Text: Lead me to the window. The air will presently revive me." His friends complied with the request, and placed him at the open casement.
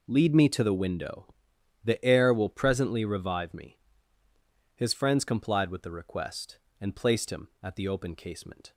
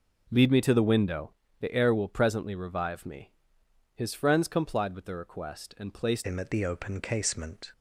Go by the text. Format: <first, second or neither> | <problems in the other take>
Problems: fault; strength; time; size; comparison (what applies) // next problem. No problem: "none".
first | changes voice at "him"; from 6.2 s on; 1.5 s long